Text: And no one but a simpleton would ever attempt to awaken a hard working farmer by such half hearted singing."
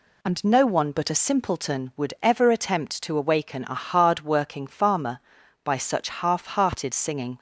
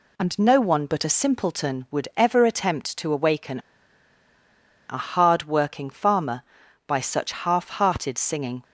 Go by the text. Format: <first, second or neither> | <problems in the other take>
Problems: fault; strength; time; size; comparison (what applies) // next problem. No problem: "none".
first | pauses between "awaken" and "a"; strong; at 3.5 s; 1.2 s long